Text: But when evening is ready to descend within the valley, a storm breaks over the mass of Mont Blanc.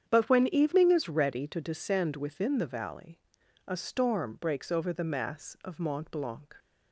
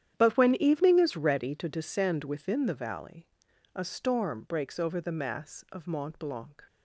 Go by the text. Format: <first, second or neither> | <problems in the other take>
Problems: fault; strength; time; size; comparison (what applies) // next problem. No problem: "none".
first | gets quieter; strong; throughout; 15.5 dB // starts louder than the rest; strong; until 1.2 s; 9.5 dB; strong in the first